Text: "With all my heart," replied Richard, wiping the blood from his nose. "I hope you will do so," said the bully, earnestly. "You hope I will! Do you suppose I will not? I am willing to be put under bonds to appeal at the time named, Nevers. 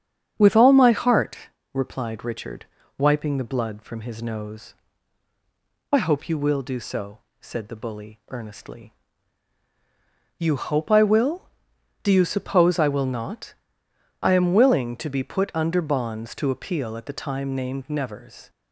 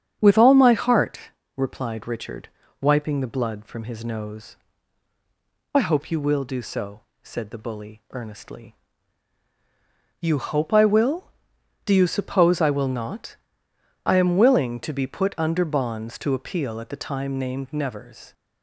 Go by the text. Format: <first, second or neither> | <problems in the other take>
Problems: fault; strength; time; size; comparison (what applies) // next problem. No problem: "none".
neither | starts louder than the rest; strong; the same in both